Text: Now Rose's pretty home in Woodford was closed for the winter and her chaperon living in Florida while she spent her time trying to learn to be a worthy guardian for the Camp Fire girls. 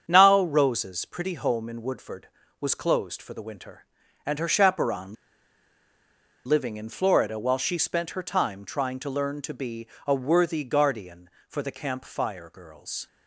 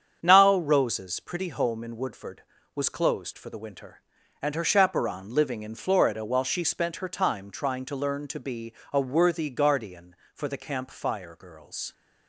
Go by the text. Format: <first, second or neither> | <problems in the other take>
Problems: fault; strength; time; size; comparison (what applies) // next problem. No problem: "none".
second | starts louder than the rest; strong; until 1.0 s; 7.5 dB; strong in the second // pauses between "chaperon" and "living"; strong; at 5.1 s; 1.3 s long // pauses between "be" and "a"; slight; at 9.8 s; 0.20 s long; slight in the second